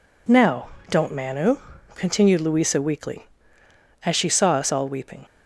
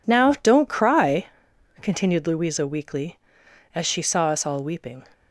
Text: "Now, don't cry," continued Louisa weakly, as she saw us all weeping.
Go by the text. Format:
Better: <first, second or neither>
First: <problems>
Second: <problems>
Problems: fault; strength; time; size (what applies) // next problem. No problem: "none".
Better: second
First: says "manu" for "cry"; at 1.1 s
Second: none